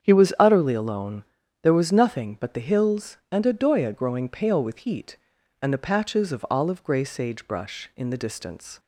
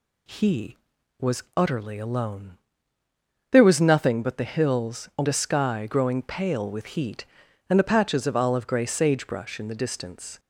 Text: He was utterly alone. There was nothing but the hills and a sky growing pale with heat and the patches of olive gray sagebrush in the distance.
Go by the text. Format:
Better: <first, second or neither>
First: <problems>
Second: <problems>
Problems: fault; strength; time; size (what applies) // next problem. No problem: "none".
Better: second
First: starts louder than the rest; strong; until 1.0 s; 8 dB // says "doya" for "sky"; at 3.5 s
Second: none